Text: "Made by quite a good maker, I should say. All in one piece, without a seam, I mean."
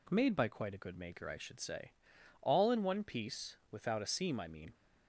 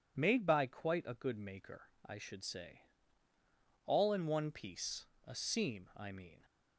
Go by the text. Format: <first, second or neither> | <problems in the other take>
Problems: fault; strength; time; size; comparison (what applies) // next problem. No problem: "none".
first | skips "without"; at 5.1 s